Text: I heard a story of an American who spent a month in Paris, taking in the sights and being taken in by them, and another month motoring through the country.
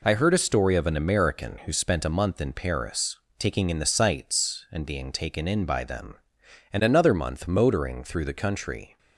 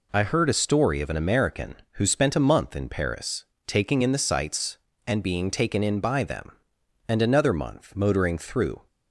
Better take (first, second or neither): first